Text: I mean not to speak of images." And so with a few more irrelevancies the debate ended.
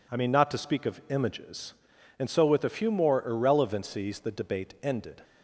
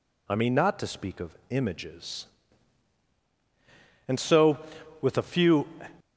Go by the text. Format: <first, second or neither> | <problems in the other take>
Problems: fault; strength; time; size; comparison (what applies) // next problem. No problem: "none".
first | pauses between "of" and "images"; slight; at 1.3 s; 0.18 s long // stops before "more irrelevancies the debate ended"; at 6.0 s